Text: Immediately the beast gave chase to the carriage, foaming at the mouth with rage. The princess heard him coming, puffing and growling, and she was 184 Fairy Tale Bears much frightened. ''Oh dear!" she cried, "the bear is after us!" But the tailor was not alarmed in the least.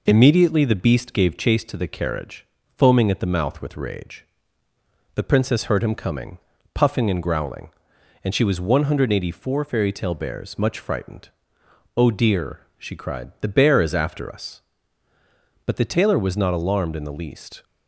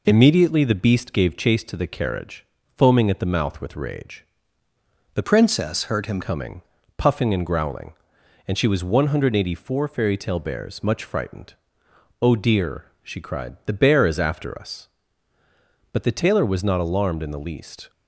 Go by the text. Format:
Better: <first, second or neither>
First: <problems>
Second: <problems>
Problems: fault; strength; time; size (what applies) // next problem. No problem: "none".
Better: first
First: none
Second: changes voice from "princess" to "him"; from 5.2 to 6.2 s; 1.0 s long